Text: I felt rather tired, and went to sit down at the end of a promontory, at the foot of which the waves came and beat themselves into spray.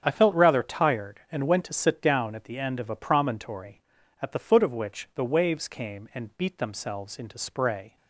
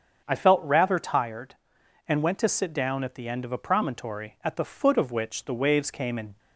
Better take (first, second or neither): first